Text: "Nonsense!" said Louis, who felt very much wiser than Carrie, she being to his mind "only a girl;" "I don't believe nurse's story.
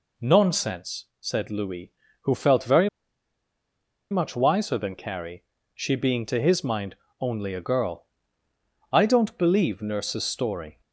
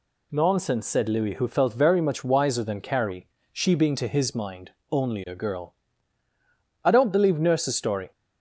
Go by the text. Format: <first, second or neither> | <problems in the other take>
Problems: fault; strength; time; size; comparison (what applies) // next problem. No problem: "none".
second | pauses between "very" and "much"; at 2.8 s; 1.2 s long // pauses between "mind" and "only"; slight; at 6.9 s; 0.24 s long; slight in the second